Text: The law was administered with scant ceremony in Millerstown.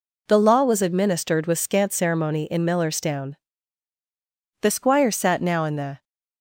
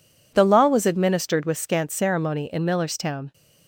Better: second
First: goes on to say "The squire sat now in the"; from 4.6 s on; 1.4 s long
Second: none

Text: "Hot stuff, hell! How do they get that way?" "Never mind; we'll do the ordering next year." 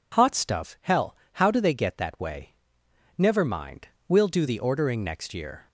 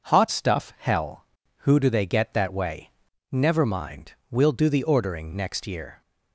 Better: first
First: none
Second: says "Who" for "How"; at 1.5 s

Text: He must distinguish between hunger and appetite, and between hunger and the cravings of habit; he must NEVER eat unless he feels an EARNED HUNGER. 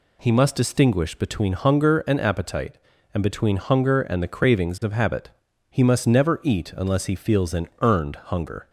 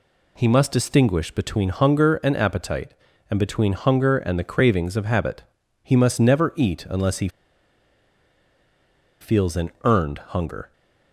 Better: first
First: none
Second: pauses between "he" and "feels"; strong; at 7.2 s; 1.9 s long

